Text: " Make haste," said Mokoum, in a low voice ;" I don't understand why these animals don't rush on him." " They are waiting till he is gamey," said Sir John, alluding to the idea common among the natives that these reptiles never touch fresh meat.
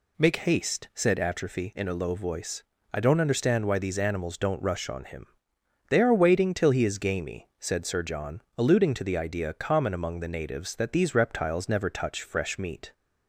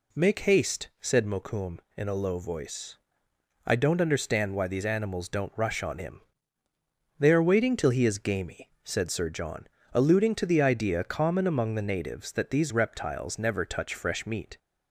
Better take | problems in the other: second | says "Atrophy" for "Mokoum"; at 1.1 s

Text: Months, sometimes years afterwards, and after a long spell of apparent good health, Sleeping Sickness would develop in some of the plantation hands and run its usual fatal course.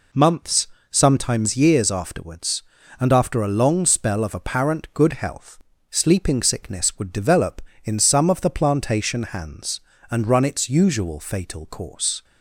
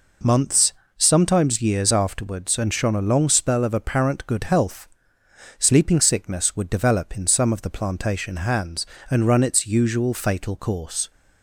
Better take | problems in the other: first | says "shone" for "after"; at 2.7 s

